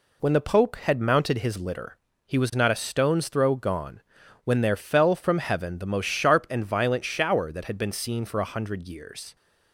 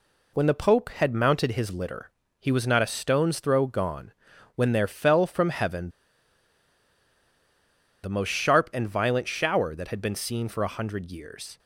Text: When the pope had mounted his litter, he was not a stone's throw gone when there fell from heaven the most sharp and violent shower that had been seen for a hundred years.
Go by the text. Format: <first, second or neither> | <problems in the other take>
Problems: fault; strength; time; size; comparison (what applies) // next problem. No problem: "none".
first | pauses between "gone" and "when"; noticeable; at 4.1 s; 0.46 s long; noticeable in the first // pauses between "heaven" and "the"; strong; at 5.9 s; 2.1 s long